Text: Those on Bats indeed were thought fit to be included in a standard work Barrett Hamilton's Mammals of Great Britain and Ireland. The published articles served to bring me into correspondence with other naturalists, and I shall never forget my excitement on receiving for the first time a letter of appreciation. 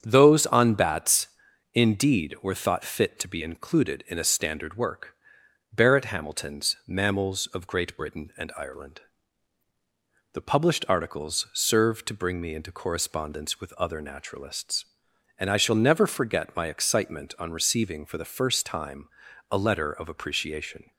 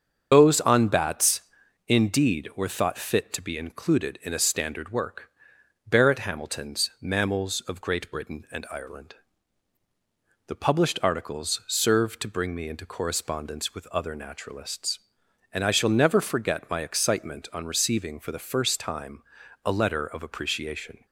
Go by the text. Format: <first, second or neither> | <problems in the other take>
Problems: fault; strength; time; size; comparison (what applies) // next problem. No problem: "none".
first | loses the start of "Those"; at 0.3 s; 150 ms // starts louder than the rest; strong; until 1.3 s; 7 dB; strong in the first // pauses between "Bats" and "indeed"; noticeable; at 1.3 s; 0.48 s long; noticeable in the first // pauses between "work" and "Barrett"; noticeable; at 5.2 s; 0.59 s long; noticeable in the first // pauses between "time" and "a"; at 19.2 s; 0.42 s long; also in the first